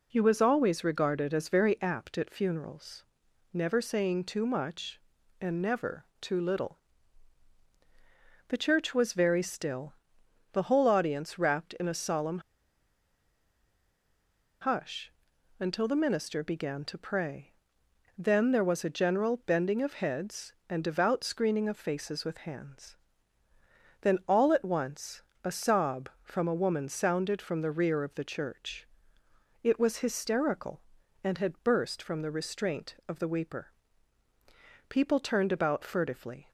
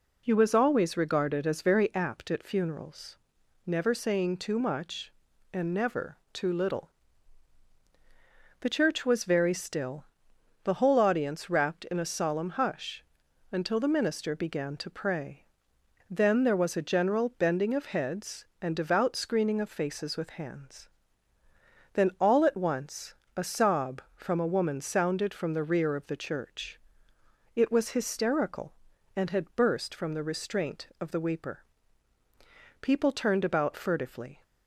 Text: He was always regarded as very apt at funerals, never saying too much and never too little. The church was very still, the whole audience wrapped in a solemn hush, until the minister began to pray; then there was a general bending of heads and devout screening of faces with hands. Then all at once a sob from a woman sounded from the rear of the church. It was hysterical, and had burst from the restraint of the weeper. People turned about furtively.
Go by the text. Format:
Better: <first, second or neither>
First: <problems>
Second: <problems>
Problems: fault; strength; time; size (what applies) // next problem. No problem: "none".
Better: second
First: pauses between "never" and "too"; slight; at 6.0 s; 0.16 s long // pauses between "solemn" and "hush"; strong; at 12.3 s; 2.2 s long // pauses between "once" and "a"; slight; at 25.2 s; 0.20 s long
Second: pauses between "never" and "too"; slight; at 6.1 s; 0.16 s long // pauses between "once" and "a"; slight; at 23.1 s; 0.20 s long